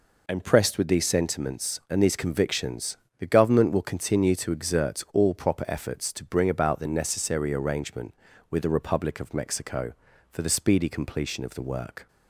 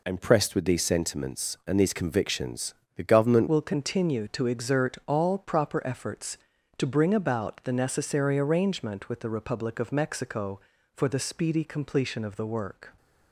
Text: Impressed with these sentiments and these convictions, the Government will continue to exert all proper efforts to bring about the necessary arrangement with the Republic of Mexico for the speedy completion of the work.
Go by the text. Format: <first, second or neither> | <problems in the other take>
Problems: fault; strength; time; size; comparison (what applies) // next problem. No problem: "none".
first | changes voice at "will"; from 3.4 s on; 9.5 s long